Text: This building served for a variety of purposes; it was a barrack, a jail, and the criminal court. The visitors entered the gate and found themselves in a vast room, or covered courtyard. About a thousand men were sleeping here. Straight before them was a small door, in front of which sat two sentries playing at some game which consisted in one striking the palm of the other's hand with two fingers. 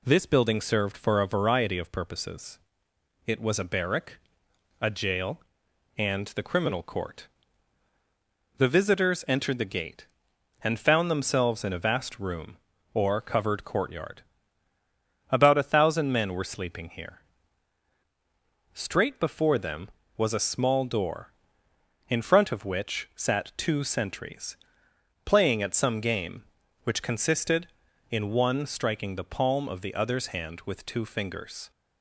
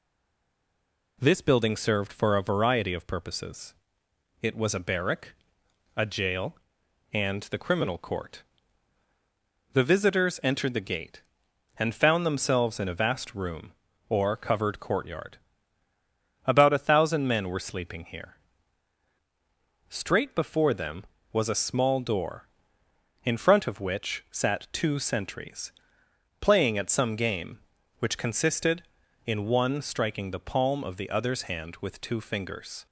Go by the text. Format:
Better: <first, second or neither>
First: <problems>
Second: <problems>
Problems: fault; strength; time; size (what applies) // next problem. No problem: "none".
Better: first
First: pauses between "sentries" and "playing"; noticeable; at 24.5 s; 0.70 s long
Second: stays silent before the first word; noticeable; until 1.1 s; 1.1 s long // pauses between "sentries" and "playing"; noticeable; at 25.7 s; 0.70 s long